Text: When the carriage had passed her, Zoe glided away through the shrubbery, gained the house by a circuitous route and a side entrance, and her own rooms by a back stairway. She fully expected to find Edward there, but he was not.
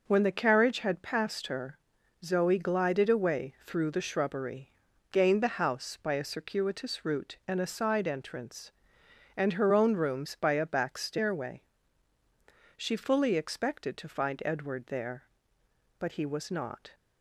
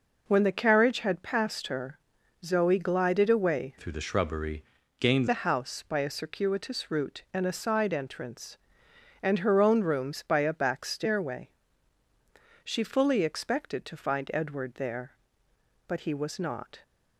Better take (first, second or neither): first